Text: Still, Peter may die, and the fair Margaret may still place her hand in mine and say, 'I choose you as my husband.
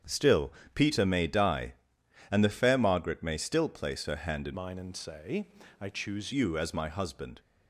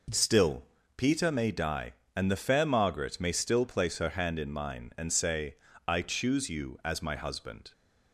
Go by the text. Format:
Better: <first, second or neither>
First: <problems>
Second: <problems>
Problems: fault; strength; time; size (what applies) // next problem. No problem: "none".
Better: second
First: starts louder than the rest; strong; until 1.2 s; 8 dB // changes voice from "mine" to "choose"; from 4.5 to 6.3 s; 1.8 s long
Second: none